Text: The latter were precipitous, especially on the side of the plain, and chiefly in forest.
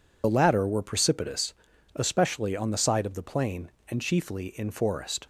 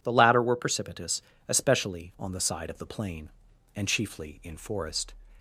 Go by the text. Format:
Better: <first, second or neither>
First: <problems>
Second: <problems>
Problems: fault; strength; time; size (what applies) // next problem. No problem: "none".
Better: second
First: loses the start of "The"; at 0.2 s; 50 ms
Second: none